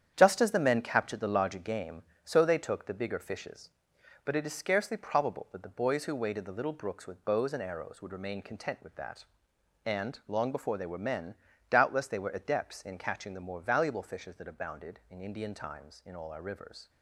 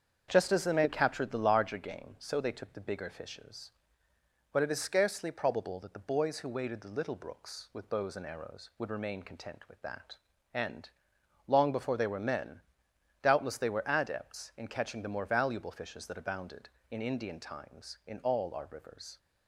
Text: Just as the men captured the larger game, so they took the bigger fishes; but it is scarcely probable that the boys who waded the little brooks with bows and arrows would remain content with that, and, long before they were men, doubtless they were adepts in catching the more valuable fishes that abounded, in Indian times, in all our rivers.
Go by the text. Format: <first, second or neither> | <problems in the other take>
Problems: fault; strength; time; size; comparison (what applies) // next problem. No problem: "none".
second | gets quieter; strong; throughout; 7.5 dB // starts louder than the rest; strong; until 1.1 s; 9 dB; strong in the second